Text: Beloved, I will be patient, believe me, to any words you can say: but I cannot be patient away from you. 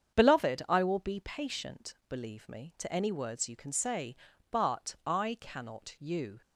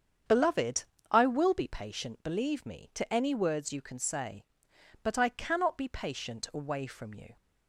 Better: second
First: starts louder than the rest; strong; until 1.2 s; 7.5 dB // skips "be patient away from"; at 5.9 s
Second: starts louder than the rest; strong; until 1.5 s; 7.5 dB

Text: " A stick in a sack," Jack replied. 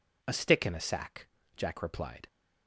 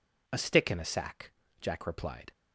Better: neither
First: none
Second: none

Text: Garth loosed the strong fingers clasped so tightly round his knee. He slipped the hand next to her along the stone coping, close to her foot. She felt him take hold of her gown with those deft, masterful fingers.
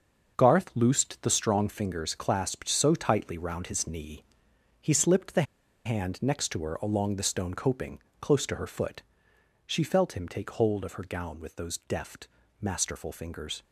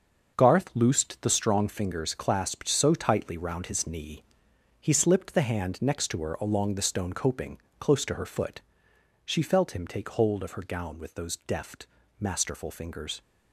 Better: second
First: starts louder than the rest; until 1.3 s; 6.5 dB // pauses between "the" and "hand"; at 5.4 s; 0.42 s long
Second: starts louder than the rest; until 1.3 s; 6.5 dB

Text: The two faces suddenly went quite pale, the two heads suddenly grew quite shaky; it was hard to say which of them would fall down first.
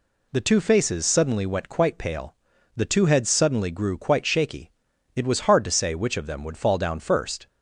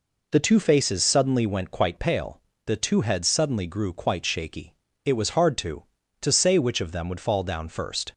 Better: first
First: none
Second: says "to" twice; at 6.2 s

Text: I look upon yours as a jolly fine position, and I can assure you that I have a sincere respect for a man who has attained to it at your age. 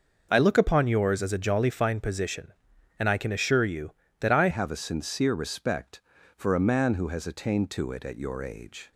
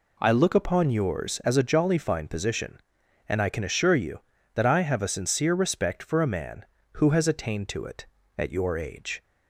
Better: second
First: changes voice at "have"; from 4.4 s on; 4.5 s long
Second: none

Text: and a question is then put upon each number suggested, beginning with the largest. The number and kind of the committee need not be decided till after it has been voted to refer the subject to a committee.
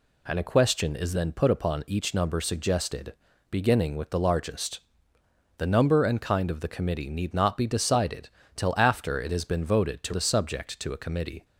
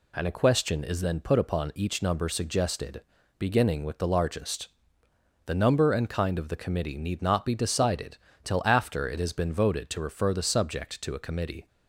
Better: second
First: pauses between "decided" and "till"; slight; at 8.2 s; 0.28 s long // skips "refer"; at 10.1 s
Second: pauses between "decided" and "till"; slight; at 8.1 s; 0.28 s long

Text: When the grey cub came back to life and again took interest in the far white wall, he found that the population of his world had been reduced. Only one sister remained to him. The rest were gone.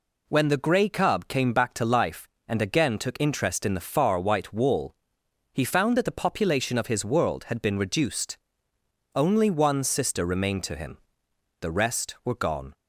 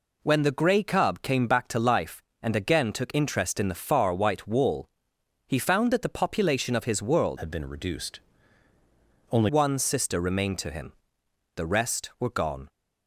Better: first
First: none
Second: changes voice from "had" to "Only"; from 7.3 to 9.4 s; 2.1 s long

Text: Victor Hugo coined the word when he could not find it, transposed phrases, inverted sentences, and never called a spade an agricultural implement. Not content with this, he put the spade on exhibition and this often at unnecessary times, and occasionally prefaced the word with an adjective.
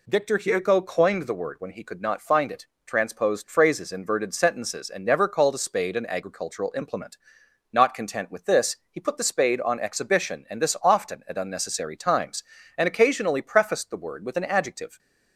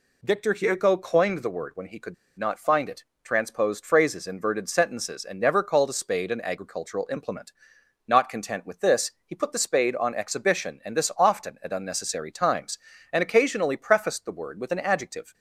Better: first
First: none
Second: pauses between "could" and "not"; slight; at 2.1 s; 0.22 s long

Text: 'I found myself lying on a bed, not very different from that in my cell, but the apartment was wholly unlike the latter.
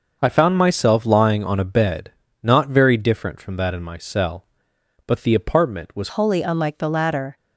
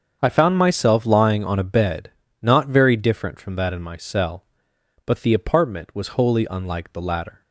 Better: second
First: starts louder than the rest; until 1.2 s; 6 dB // changes voice at "wholly"; from 6.0 s on; 1.3 s long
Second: starts louder than the rest; strong; until 1.2 s; 7 dB

